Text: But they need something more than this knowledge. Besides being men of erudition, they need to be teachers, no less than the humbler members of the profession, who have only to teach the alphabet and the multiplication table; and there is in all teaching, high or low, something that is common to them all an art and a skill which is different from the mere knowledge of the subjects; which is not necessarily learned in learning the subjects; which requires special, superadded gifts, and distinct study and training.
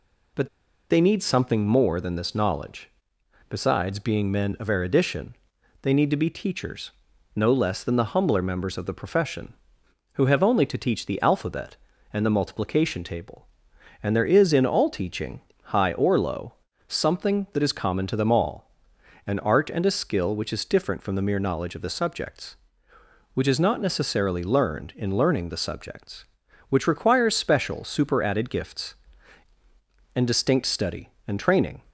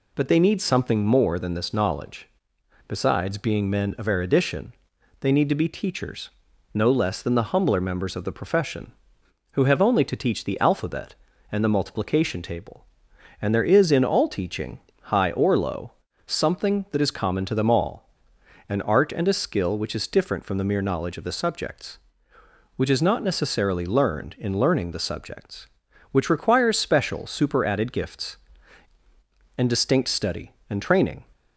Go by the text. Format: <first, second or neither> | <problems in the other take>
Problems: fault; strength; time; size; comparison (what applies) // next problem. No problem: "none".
second | pauses between "But" and "they"; at 0.4 s; 0.42 s long // pauses between "all" and "an"; noticeable; at 18.6 s; 0.56 s long; noticeable in the second